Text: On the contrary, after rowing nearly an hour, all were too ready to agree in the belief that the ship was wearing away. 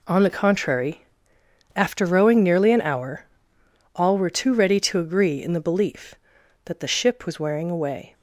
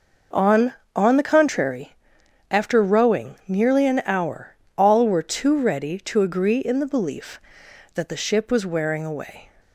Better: first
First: none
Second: says "On" twice; at 0.9 s

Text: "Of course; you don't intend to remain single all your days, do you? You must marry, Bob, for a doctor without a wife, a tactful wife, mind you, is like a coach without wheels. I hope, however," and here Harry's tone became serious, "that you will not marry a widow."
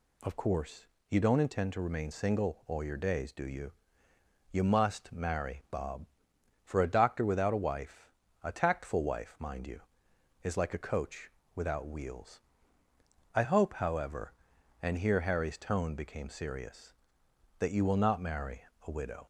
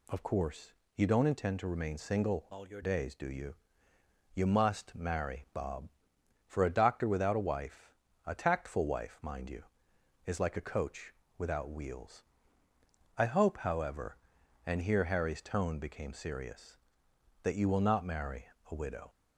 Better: first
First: pauses between "coach" and "without"; slight; at 11.3 s; 0.24 s long // pauses between "marry" and "a"; slight; at 18.6 s; 0.24 s long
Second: changes voice from "all" to "your"; from 2.5 to 2.8 s; 0.3 s long // pauses between "coach" and "without"; slight; at 11.1 s; 0.24 s long // pauses between "marry" and "a"; slight; at 18.4 s; 0.24 s long

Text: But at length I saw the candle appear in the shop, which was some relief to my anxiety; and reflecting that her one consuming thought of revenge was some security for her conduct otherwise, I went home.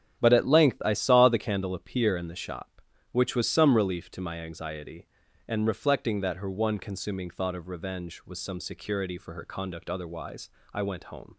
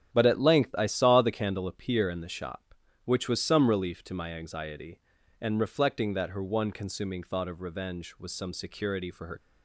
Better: first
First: starts louder than the rest; strong; until 1.2 s; 9.5 dB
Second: starts louder than the rest; strong; until 1.1 s; 9.5 dB // stops before "conduct otherwise I went home"; at 9.3 s

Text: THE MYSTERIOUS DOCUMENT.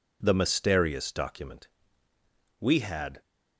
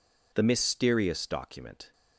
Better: second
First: goes on to say "WE had"; noticeable; from 2.5 s on; 0.62 s long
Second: none

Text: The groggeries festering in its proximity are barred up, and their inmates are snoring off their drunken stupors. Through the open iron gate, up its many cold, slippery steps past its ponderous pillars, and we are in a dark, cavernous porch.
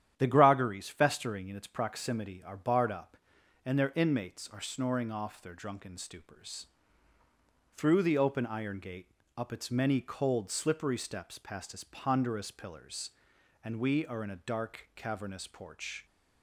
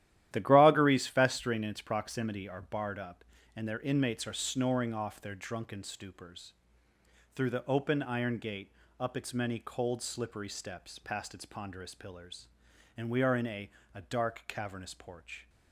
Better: first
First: starts louder than the rest; strong; until 1.1 s; 10.5 dB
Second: starts louder than the rest; strong; until 1.3 s; 12.5 dB // says "a" twice; at 13.9 s

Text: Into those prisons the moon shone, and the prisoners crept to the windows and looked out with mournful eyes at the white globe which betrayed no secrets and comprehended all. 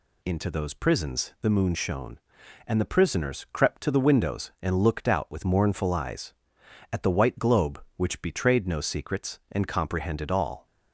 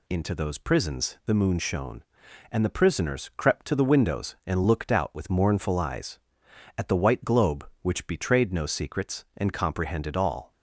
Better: neither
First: none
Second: none

